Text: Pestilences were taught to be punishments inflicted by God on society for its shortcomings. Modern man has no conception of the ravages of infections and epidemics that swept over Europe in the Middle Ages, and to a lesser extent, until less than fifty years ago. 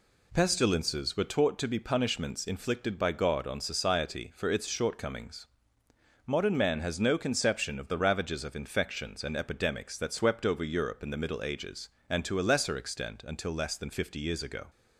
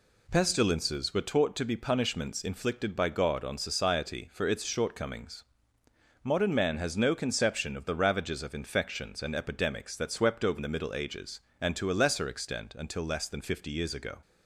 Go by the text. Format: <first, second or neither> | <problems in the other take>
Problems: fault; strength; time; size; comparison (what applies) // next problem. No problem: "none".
first | skips "Europe in"; at 10.5 s